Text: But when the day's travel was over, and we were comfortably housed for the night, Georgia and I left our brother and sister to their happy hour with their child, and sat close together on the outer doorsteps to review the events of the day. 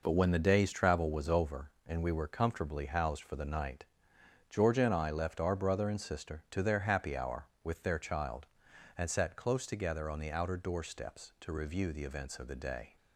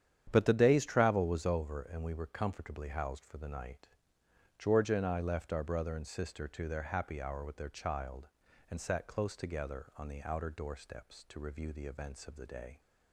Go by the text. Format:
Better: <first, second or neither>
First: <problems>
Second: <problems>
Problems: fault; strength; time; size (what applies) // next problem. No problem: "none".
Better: first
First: none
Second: starts louder than the rest; strong; until 1.3 s; 9.5 dB // skips "when"; at 0.4 s